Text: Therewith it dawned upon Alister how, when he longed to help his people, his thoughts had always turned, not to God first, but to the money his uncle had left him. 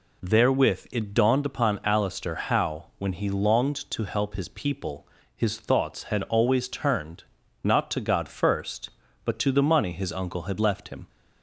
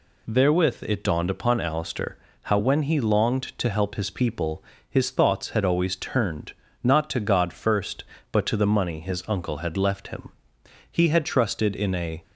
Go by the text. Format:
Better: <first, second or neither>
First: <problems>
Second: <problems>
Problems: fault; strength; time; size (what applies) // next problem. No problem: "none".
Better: first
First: none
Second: pauses between "Alister" and "how"; slight; at 2.1 s; 0.26 s long // goes on to say "He had trusted in a"; from 10.8 s on; 1.3 s long